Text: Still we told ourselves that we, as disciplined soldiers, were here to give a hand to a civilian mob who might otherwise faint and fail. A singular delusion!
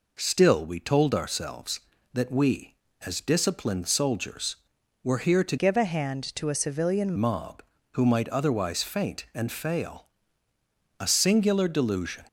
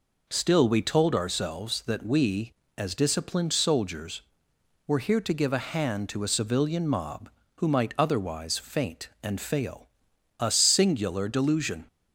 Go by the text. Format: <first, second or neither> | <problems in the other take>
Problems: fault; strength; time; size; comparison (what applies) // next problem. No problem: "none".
second | changes voice from "give" to "civilian"; from 5.5 to 7.1 s; 1.6 s long